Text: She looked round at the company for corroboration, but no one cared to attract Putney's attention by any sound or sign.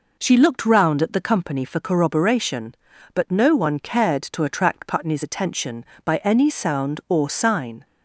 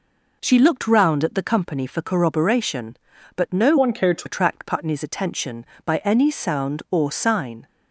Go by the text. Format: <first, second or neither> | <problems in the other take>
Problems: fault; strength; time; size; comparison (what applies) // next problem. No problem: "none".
first | changes voice from "one" to "to"; from 3.7 to 4.2 s; 0.5 s long